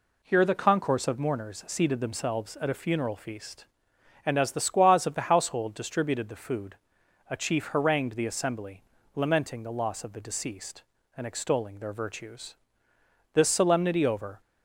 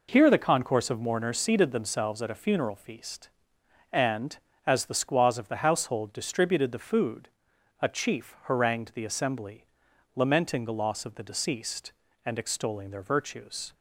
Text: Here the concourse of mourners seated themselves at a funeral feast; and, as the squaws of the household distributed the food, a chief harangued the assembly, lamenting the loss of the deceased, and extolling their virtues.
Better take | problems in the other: second | goes on to say "This solemnity over"; noticeable; from 13.3 s on; 1.0 s long

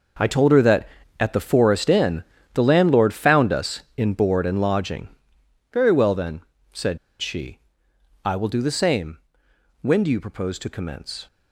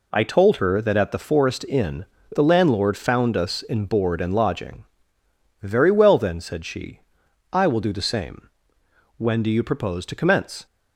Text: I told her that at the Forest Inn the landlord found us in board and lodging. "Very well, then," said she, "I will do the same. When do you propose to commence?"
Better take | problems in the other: second | pauses between "Inn" and "the"; slight; at 2.2 s; 0.30 s long; slight in the second // pauses between "said" and "she"; slight; at 6.9 s; 0.22 s long

